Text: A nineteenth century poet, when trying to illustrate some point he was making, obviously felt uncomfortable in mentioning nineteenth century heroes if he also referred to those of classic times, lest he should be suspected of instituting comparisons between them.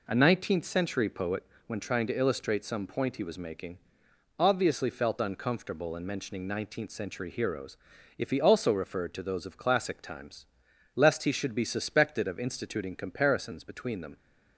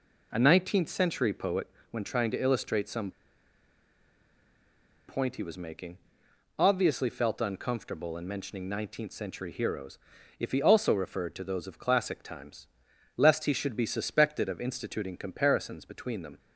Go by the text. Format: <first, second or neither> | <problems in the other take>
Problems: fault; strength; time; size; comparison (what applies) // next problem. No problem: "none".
first | pauses between "some" and "point"; strong; at 3.1 s; 1.9 s long // pauses between "heroes" and "if"; at 9.9 s; 0.42 s long; also in the first